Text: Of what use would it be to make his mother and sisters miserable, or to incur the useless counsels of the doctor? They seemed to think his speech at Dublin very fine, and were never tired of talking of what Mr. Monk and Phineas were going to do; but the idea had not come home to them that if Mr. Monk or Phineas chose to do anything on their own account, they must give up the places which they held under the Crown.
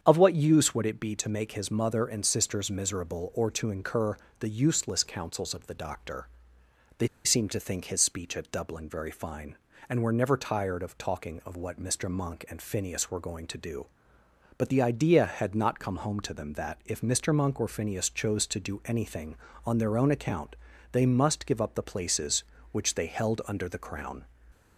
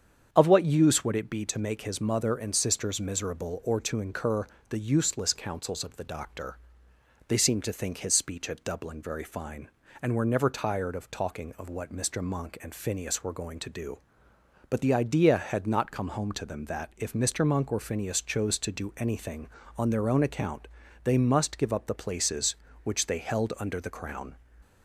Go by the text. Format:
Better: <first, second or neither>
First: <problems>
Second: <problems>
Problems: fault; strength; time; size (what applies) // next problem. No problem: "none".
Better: second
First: starts louder than the rest; strong; until 1.0 s; 8 dB // pauses between "incur" and "the"; slight; at 4.1 s; 0.22 s long // pauses between "They" and "seemed"; slight; at 7.0 s; 0.17 s long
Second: starts louder than the rest; strong; until 1.3 s; 8 dB // pauses between "incur" and "the"; slight; at 4.4 s; 0.22 s long